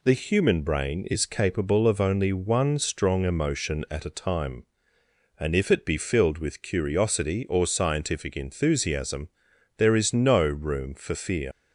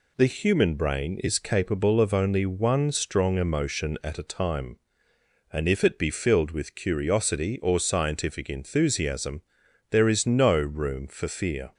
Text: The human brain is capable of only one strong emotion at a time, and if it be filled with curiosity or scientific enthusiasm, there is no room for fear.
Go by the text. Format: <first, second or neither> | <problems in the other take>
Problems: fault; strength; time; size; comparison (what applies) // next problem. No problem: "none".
second | leaves "fear" unfinished; at 11.5 s; 95 ms